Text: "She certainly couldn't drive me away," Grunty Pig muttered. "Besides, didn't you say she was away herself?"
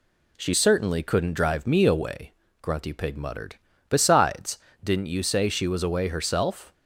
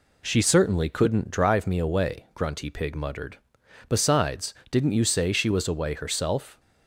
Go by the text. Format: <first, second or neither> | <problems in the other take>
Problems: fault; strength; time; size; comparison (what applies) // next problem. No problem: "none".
neither | none